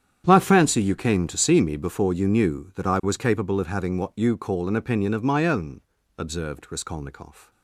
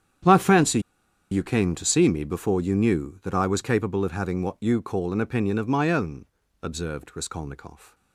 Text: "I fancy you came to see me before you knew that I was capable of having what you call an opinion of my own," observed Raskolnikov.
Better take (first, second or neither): first